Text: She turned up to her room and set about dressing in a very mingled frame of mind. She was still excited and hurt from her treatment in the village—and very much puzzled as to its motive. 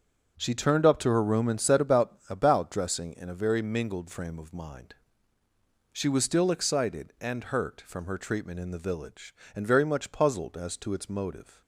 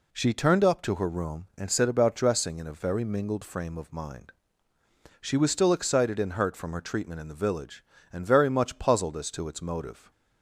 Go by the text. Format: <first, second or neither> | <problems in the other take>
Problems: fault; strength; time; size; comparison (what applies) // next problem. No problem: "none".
second | starts louder than the rest; until 1.3 s; 7 dB // says "about" twice; at 2.2 s